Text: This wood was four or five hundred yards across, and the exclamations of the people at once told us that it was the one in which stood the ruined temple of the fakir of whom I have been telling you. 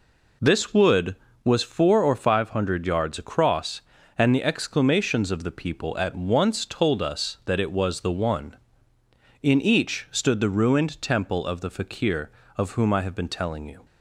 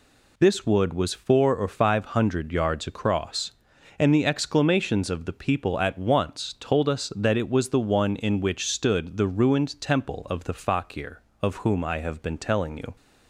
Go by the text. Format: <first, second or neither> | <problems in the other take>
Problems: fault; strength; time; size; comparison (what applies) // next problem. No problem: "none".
second | says "each" for "which"; at 9.6 s